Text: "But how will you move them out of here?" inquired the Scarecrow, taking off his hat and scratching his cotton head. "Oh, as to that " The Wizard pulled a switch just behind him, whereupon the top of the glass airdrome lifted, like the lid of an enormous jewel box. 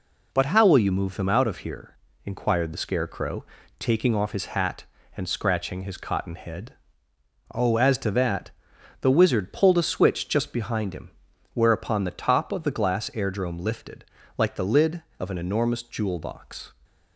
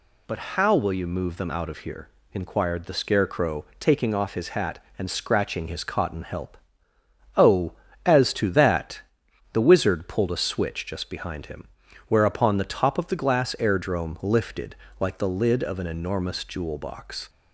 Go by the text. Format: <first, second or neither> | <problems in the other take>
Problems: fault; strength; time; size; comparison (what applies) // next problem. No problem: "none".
first | pauses between "But" and "how"; slight; at 0.3 s; 0.16 s long // says "help" for "head"; at 6.2 s